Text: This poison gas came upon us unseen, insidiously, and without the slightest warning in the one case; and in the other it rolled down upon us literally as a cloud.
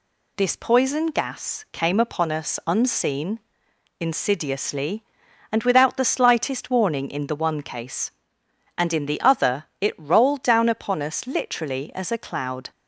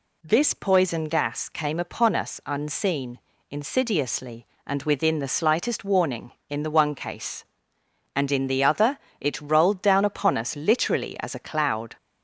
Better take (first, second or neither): first